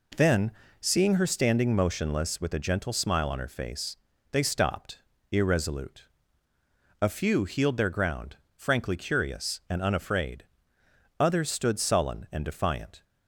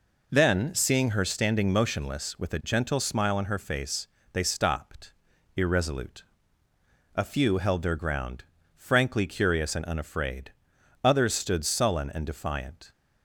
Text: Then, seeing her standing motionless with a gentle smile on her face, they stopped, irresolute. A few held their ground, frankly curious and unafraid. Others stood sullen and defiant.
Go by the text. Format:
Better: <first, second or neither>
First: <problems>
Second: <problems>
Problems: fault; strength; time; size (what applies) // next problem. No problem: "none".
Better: second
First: says "healed" for "held"; at 7.4 s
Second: none